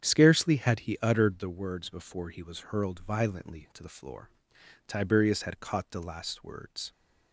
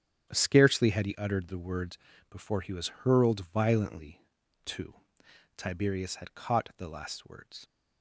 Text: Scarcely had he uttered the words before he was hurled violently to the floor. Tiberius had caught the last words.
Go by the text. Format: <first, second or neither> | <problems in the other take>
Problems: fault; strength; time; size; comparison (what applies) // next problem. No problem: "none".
first | starts louder than the rest; strong; until 1.3 s; 9.5 dB; strong in the first // pauses between "words" and "before"; slight; at 1.9 s; 0.34 s long // skips "the floor"; at 5.2 s